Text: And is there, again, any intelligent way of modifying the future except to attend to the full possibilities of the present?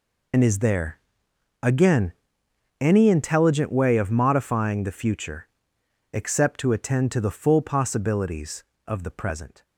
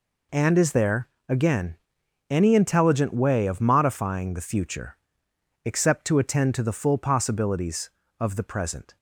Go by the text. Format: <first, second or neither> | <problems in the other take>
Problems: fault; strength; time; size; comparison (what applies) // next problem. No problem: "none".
second | loses the start of "And"; at 0.3 s; 60 ms // pauses between "future" and "except"; noticeable; at 5.4 s; 0.64 s long; noticeable in the second